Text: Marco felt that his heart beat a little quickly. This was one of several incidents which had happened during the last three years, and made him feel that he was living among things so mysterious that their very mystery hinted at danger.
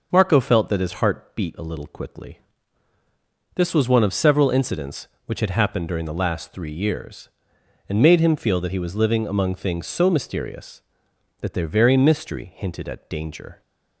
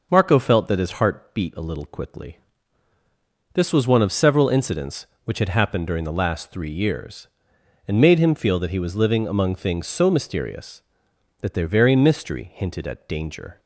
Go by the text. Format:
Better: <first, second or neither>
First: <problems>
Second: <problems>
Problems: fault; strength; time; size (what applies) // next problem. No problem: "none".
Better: neither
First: none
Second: none